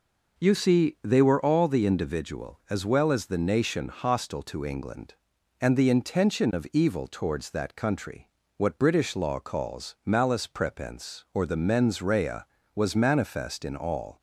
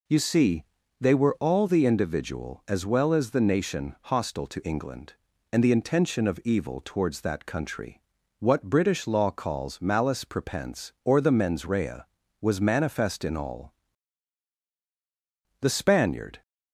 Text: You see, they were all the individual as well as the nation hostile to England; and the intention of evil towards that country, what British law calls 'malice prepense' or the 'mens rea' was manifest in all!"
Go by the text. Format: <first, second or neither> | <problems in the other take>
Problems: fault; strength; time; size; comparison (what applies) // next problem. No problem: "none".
first | goes on to say "The Spaniard"; noticeable; from 15.6 s on; 0.80 s long